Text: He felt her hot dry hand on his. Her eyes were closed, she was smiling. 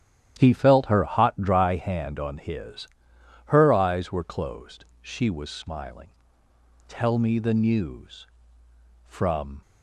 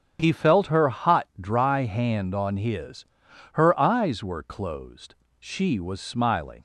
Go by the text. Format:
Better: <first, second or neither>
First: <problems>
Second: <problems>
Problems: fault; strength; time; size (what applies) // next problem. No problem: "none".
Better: second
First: starts louder than the rest; strong; until 1.3 s; 11 dB // goes on to say "Tell me the news from"; strong; from 6.8 s on; 2.7 s long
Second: starts louder than the rest; strong; until 1.2 s; 7.5 dB